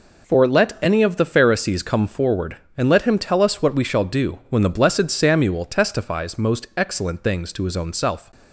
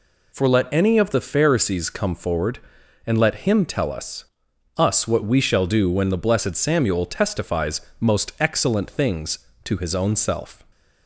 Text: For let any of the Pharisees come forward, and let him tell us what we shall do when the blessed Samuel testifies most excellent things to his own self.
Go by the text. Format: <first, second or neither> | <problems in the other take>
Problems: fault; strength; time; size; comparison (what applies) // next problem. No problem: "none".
first | says "us" twice; at 4.7 s // pauses between "testifies" and "most"; slight; at 7.7 s; 0.20 s long